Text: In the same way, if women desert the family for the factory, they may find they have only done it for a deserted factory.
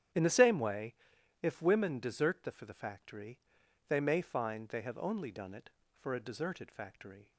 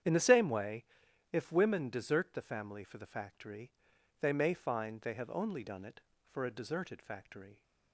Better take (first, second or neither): second